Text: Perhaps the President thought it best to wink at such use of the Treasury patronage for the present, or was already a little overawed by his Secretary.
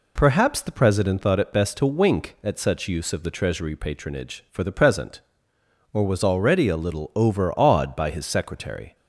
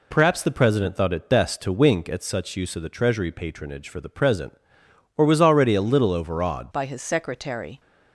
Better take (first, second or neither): first